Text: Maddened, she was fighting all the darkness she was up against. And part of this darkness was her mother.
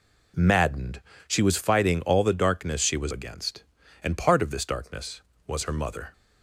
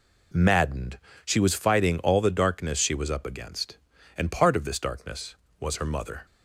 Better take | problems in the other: second | skips "up"; at 3.1 s

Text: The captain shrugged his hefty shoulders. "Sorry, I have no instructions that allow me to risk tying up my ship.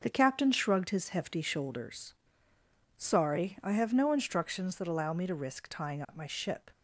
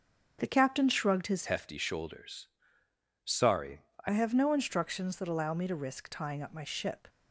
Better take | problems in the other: first | starts louder than the rest; until 1.4 s; 6.5 dB; also in the first // changes voice from "hefty" to "I"; from 1.4 to 4.0 s; 2.6 s long

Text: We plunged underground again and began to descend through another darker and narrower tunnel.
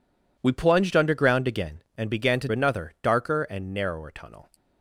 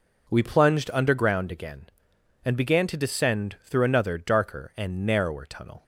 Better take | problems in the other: second | skips "descend through"; at 2.4 s

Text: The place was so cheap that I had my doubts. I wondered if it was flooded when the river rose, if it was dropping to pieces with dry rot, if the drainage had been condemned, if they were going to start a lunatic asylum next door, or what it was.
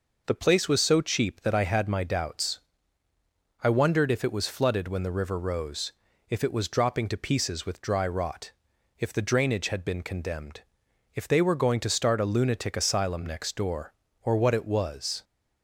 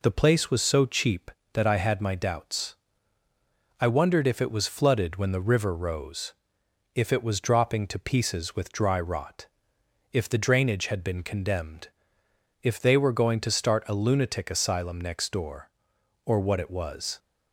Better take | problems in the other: neither | none

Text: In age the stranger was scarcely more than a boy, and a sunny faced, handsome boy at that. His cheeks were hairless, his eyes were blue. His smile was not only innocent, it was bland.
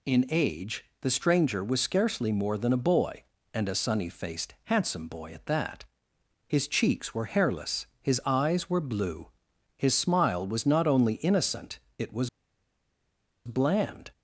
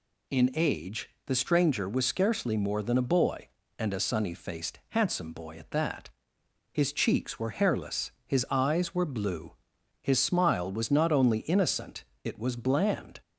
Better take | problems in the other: second | pauses between "age" and "the"; slight; at 0.8 s; 0.16 s long; slight in the second // pauses between "was" and "bland"; at 12.2 s; 1.1 s long

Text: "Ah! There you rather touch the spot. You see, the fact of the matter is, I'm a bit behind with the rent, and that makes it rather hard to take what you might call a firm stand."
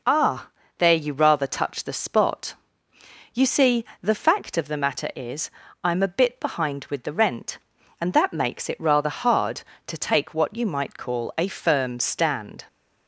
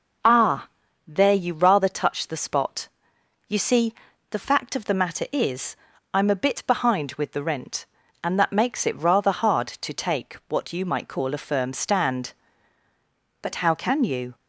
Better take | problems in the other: first | goes on to say "But how can you"; noticeable; from 13.4 s on; 0.94 s long

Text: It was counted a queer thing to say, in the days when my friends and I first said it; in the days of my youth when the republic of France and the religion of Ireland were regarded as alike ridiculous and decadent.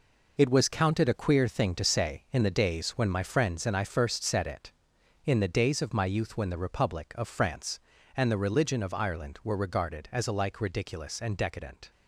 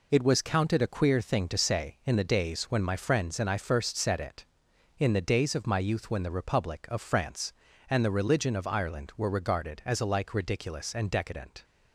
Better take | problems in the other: second | gets quieter; strong; throughout; 8.5 dB

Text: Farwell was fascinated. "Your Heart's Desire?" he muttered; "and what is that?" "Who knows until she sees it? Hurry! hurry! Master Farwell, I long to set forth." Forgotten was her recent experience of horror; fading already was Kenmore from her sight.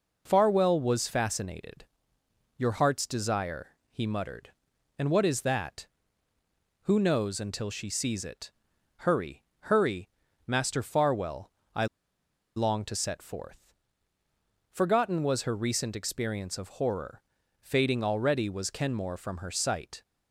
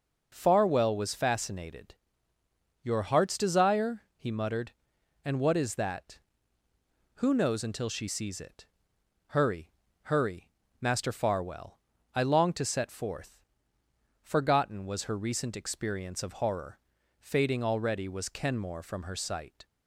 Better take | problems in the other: second | pauses between "I" and "long"; noticeable; at 11.8 s; 0.69 s long

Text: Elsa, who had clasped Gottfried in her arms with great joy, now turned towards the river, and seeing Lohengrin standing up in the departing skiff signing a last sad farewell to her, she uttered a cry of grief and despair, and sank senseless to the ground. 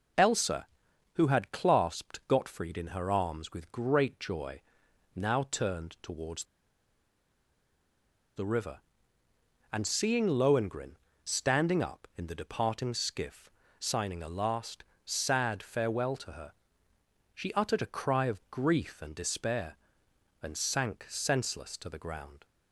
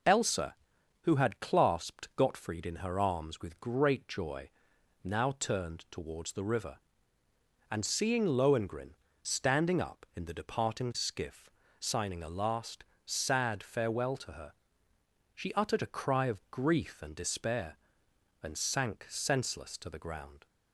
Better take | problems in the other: second | pauses between "towards" and "the"; strong; at 6.4 s; 1.9 s long // pauses between "Lohengrin" and "standing"; slight; at 10.9 s; 0.26 s long; slight in the second // pauses between "skiff" and "signing"; slight; at 13.4 s; 0.30 s long; slight in the second // pauses between "last" and "sad"; slight; at 14.8 s; 0.22 s long; slight in the second

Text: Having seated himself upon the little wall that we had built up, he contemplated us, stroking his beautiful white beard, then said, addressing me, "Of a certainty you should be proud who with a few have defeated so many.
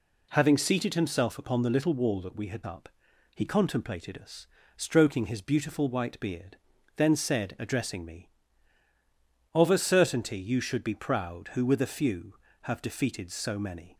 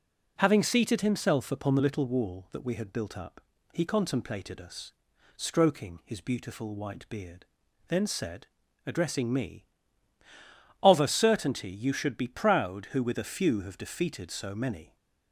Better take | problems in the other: second | skips "built"; at 2.6 s

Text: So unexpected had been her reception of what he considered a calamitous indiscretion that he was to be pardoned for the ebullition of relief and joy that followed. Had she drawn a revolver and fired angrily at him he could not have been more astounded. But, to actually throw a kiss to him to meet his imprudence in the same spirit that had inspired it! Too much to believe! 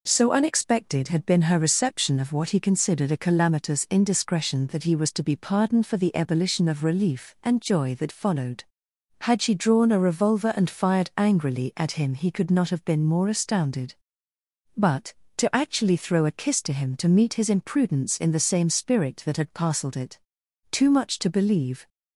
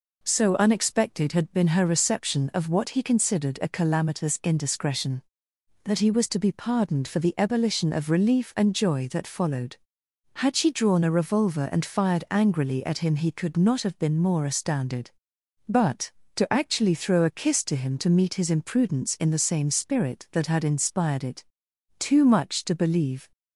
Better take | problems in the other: second | says "parcelled" for "inspired"; at 19.5 s

